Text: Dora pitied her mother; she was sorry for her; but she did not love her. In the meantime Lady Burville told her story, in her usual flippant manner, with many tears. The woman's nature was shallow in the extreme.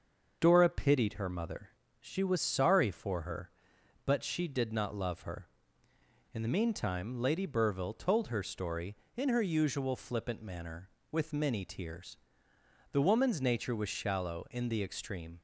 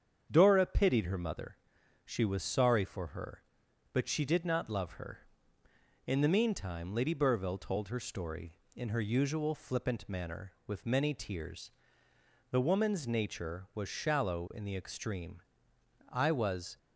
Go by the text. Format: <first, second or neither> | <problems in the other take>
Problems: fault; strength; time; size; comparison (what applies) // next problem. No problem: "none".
first | starts louder than the rest; strong; until 1.3 s; 7.5 dB; also in the first // goes on to say "I was"; noticeable; from 16.0 s on; 0.68 s long